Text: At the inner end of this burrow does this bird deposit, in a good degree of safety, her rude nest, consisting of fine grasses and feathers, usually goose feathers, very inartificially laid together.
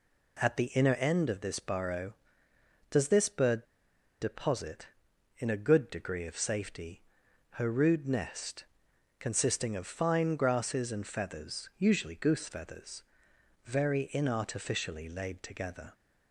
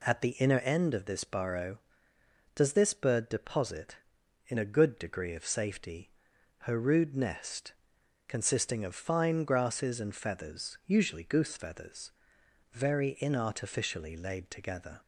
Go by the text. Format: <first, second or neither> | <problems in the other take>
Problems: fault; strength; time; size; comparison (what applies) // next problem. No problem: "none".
second | pauses between "bird" and "deposit"; noticeable; at 3.6 s; 0.57 s long